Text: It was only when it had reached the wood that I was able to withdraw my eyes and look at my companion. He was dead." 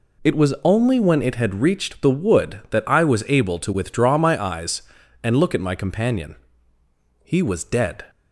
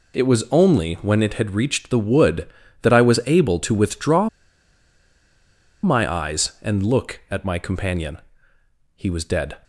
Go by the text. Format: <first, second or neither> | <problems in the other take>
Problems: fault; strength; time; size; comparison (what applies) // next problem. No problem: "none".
first | pauses between "withdraw" and "my"; strong; at 4.2 s; 1.5 s long